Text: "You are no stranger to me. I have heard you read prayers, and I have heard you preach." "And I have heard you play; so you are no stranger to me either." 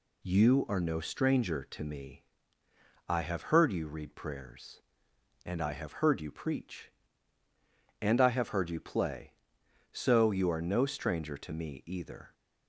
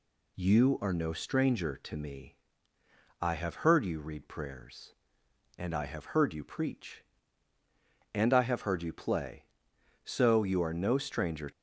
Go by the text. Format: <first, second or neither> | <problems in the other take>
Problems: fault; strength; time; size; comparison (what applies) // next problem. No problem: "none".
first | stops before "to me either"; at 11.5 s